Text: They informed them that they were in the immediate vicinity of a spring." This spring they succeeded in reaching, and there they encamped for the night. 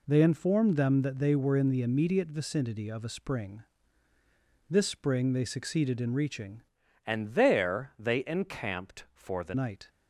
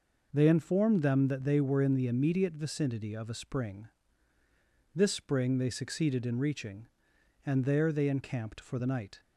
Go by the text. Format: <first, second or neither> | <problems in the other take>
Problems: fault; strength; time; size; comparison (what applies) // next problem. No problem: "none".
second | changes voice from "and" to "the"; from 7.0 to 9.5 s; 2.5 s long